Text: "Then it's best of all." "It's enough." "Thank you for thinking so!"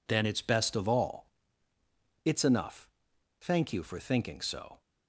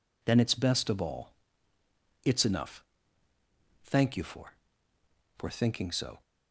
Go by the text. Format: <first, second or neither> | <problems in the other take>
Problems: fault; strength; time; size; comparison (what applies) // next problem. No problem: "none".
first | says "for" twice; at 5.3 s